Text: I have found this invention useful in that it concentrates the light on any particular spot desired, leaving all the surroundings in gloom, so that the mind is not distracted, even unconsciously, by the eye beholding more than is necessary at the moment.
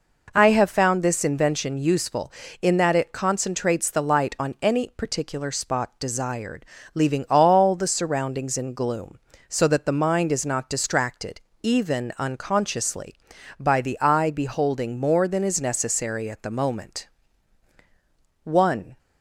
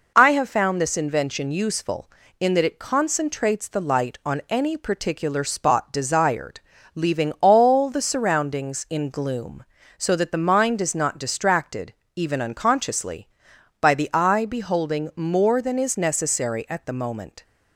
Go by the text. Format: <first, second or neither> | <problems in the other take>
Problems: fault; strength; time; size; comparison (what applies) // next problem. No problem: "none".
second | goes on to say "One"; from 18.4 s on; 0.54 s long